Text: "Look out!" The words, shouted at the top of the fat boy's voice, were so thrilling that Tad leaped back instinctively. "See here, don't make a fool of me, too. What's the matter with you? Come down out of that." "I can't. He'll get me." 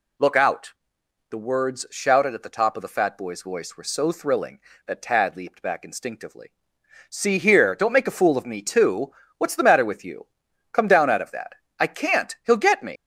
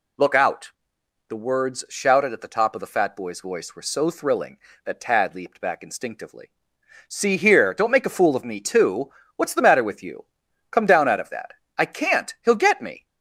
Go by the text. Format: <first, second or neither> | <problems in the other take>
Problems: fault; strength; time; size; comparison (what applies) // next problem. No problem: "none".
second | leaves "me" unfinished; at 12.9 s; 115 ms